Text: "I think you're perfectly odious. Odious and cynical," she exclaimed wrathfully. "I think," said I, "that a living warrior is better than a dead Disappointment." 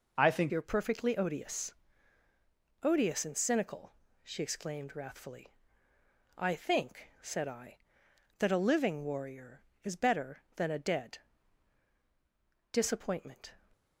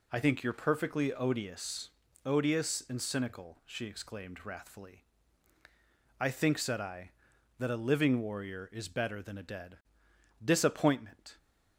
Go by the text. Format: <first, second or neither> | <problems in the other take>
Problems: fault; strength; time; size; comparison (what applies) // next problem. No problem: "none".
second | changes voice at "you're"; from 0.4 s on; 13.1 s long // pauses between "dead" and "Disappointment"; strong; at 11.1 s; 1.5 s long; noticeable in the second